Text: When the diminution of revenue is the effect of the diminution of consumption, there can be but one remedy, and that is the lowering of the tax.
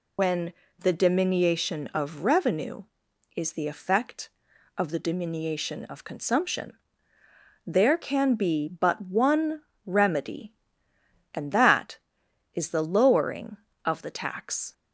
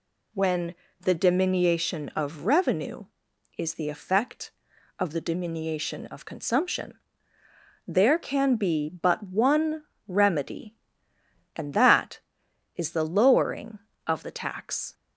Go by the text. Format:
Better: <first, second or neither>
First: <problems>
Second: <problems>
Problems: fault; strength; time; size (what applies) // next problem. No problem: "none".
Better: second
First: loses the start of "When"; at 0.1 s; 70 ms // pauses between "When" and "the"; slight; at 0.5 s; 0.26 s long // pauses between "one" and "remedy"; slight; at 9.6 s; 0.24 s long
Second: pauses between "When" and "the"; slight; at 0.7 s; 0.26 s long // pauses between "one" and "remedy"; slight; at 9.8 s; 0.24 s long